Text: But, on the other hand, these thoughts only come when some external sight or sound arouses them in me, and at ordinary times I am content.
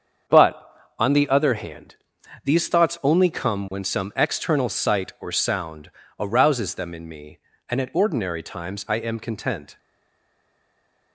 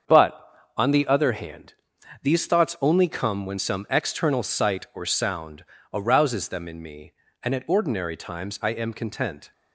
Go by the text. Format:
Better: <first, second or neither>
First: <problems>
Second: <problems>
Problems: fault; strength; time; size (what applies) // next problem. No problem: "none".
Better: second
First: starts louder than the rest; strong; until 1.6 s; 7.5 dB // pauses between "sound" and "arouses"; slight; at 5.8 s; 0.28 s long // stays silent after the last word; noticeable; from 9.7 s on; 1.4 s long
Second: starts louder than the rest; strong; until 1.4 s; 7.5 dB // pauses between "sound" and "arouses"; slight; at 5.6 s; 0.28 s long